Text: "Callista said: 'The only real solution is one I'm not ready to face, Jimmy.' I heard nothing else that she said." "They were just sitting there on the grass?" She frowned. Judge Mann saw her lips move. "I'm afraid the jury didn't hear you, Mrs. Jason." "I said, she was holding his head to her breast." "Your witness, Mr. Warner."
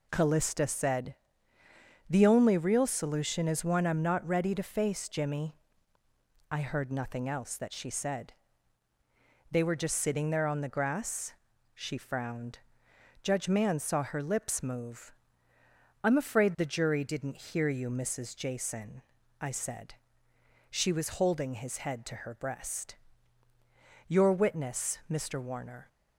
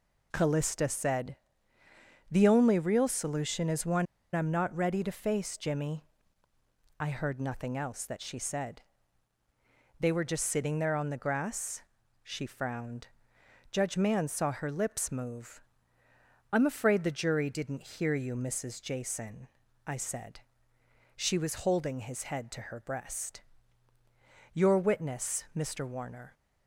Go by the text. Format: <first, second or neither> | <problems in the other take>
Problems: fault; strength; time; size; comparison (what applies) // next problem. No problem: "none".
first | pauses between "one" and "I'm"; slight; at 4.0 s; 0.27 s long